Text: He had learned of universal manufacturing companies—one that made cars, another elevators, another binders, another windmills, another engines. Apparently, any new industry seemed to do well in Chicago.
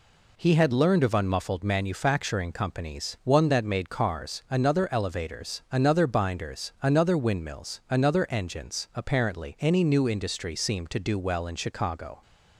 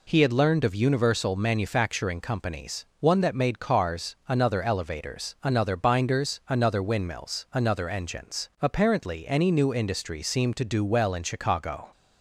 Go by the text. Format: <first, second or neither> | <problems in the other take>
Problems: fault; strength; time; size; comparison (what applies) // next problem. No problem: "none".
second | says "unmuffled" for "universal"; at 1.1 s